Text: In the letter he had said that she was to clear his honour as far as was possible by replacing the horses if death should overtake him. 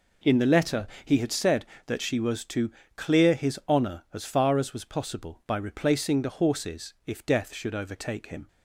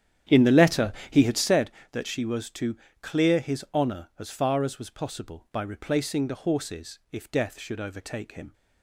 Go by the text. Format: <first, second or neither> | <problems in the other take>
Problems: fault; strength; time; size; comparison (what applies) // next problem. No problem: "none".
first | starts louder than the rest; strong; until 1.8 s; 10 dB // pauses between "letter" and "he"; slight; at 0.9 s; 0.18 s long; slight in the first // pauses between "to" and "clear"; slight; at 2.7 s; 0.24 s long; slight in the first